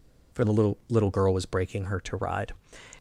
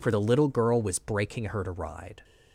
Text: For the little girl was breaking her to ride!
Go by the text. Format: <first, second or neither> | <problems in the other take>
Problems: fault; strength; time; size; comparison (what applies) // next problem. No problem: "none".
second | says "little" twice; at 0.8 s